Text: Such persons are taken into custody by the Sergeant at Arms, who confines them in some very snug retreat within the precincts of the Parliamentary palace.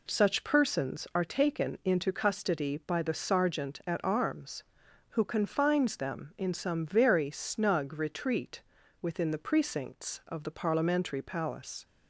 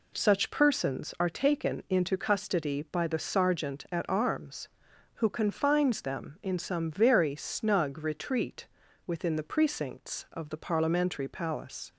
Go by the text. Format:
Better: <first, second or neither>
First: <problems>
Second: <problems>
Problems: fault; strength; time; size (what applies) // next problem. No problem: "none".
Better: neither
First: pauses between "retreat" and "within"; at 8.6 s; 0.40 s long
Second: pauses between "retreat" and "within"; at 8.6 s; 0.40 s long